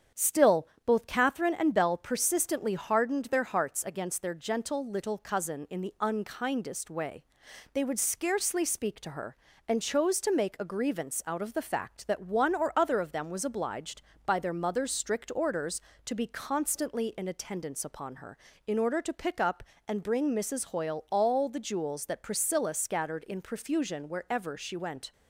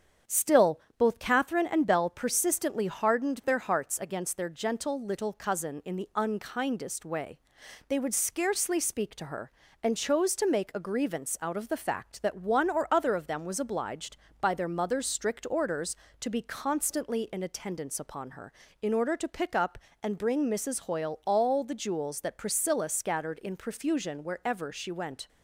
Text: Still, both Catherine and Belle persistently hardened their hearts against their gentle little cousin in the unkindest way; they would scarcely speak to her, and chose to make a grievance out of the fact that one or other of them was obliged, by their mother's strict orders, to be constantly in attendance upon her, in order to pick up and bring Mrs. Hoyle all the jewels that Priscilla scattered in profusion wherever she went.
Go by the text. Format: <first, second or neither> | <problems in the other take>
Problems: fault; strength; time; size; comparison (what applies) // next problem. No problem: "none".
neither | starts louder than the rest; strong; the same in both